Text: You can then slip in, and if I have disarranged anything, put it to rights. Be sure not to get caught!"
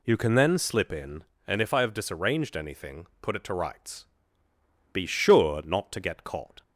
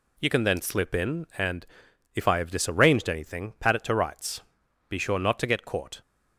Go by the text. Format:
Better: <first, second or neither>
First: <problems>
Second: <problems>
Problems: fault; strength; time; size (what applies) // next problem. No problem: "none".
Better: first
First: none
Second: pauses between "and" and "if"; noticeable; at 1.6 s; 0.50 s long // says "pat" for "put"; at 3.5 s